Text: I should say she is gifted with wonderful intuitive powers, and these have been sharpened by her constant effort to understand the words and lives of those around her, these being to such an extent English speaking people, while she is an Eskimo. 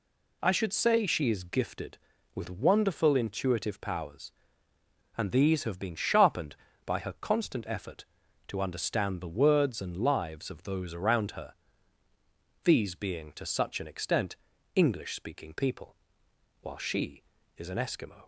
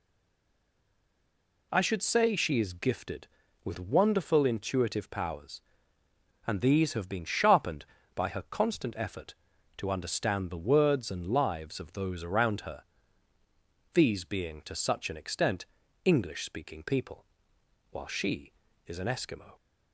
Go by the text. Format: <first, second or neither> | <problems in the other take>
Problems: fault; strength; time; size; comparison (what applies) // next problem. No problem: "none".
first | stays silent before the first word; noticeable; until 1.7 s; 1.7 s long // pauses between "extent" and "English"; at 15.6 s; 0.40 s long; also in the first